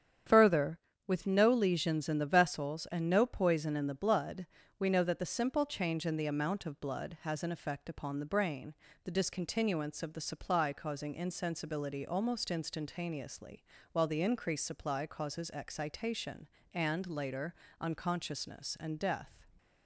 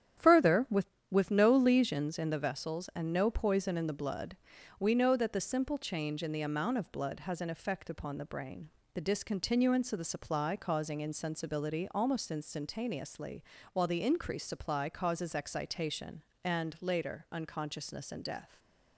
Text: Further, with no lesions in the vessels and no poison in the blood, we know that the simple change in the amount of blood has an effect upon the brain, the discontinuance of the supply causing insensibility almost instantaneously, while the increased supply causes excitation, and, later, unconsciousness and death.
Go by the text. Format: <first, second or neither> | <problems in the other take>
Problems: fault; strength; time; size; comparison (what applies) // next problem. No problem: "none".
first | starts louder than the rest; strong; until 1.4 s; 10 dB; strong in the first // says "with" twice; at 1.1 s